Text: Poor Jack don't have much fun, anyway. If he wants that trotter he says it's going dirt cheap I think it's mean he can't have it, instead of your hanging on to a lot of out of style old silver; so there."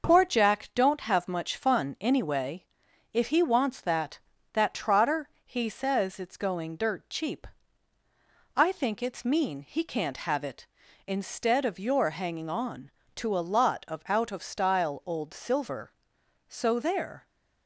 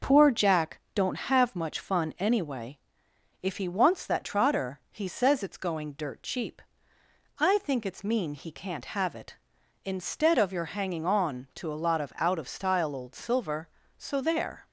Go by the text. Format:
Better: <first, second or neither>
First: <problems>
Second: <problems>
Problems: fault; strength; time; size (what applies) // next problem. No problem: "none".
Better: second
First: starts louder than the rest; noticeable; until 1.1 s; 6 dB // says "that" twice; at 4.5 s // pauses between "cheap" and "I"; at 7.4 s; 1.0 s long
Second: pauses between "cheap" and "I"; noticeable; at 6.6 s; 0.78 s long